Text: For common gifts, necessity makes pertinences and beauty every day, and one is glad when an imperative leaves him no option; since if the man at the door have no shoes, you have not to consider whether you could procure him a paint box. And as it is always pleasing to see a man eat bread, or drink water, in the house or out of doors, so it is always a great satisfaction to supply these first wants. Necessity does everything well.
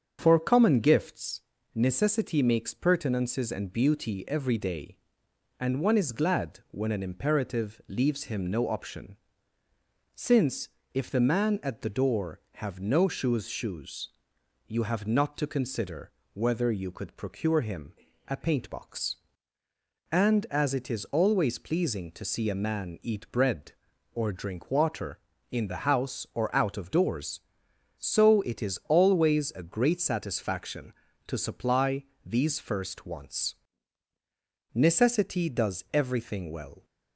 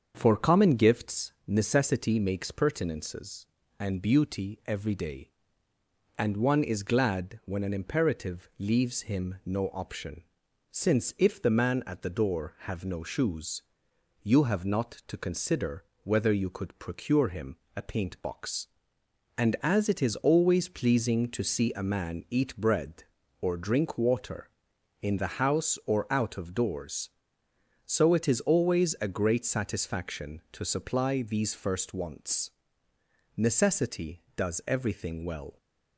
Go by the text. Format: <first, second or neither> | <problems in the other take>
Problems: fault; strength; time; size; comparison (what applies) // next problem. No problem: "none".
second | starts louder than the rest; strong; until 1.2 s; 7.5 dB; also in the second // pauses between "since" and "if"; slight; at 10.6 s; 0.24 s long // says "shoes" twice; at 13.4 s // pauses between "consider" and "whether"; slight; at 16.1 s; 0.22 s long; slight in the second // pauses between "him" and "a"; slight; at 17.9 s; 0.34 s long; slight in the second // pauses between "supply" and "these"; slight; at 32.0 s; 0.20 s long